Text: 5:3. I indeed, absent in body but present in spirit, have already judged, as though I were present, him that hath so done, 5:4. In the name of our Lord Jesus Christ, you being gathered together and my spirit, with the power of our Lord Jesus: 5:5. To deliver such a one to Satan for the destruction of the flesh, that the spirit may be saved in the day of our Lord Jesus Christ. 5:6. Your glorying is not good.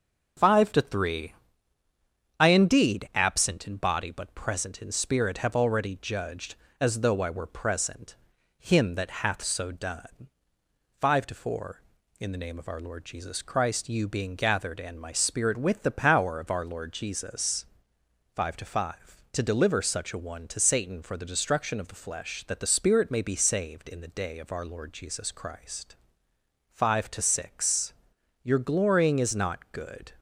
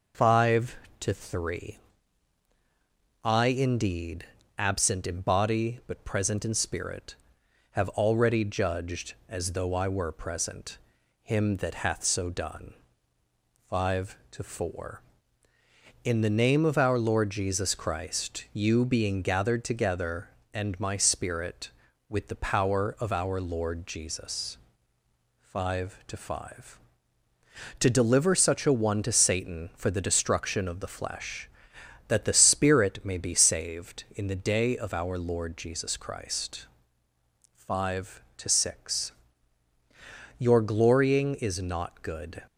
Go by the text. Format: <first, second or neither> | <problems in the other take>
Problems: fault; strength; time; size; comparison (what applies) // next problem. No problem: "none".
second | starts louder than the rest; strong; until 2.4 s; 7.5 dB // skips "together"; at 14.7 s